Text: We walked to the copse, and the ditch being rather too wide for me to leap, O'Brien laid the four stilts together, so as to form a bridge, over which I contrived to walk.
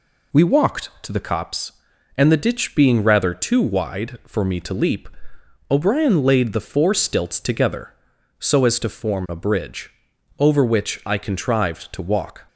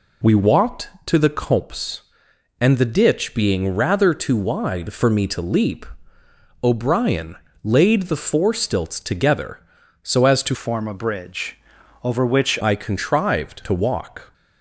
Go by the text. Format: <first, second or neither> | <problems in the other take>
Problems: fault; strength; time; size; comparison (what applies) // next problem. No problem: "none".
first | pauses between "O'Brien" and "laid"; slight; at 7.3 s; 0.30 s long // changes voice from "form" to "which"; from 10.5 to 12.5 s; 2.0 s long